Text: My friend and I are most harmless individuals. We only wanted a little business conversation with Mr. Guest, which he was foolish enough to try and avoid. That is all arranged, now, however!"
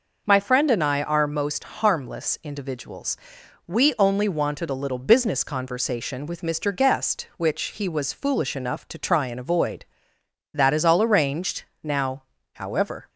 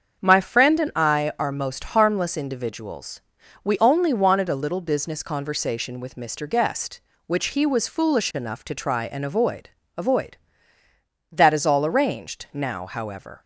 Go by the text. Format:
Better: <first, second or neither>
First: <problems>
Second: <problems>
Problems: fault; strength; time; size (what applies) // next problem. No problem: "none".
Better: first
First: none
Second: starts louder than the rest; until 1.2 s; 7 dB // says "avoid" twice; at 9.9 s